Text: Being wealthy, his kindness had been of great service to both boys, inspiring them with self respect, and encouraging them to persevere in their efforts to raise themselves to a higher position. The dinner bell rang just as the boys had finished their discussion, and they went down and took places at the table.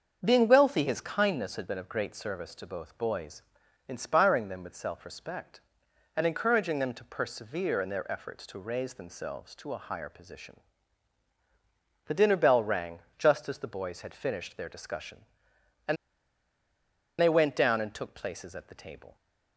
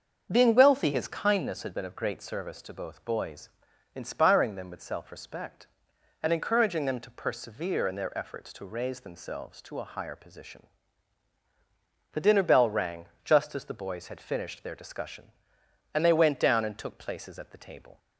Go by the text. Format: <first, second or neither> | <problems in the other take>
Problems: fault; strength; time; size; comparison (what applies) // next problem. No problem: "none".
second | starts louder than the rest; until 1.2 s; 7 dB; also in the second // pauses between "rang" and "just"; slight; at 12.9 s; 0.18 s long; slight in the second // pauses between "and" and "they"; at 15.9 s; 1.2 s long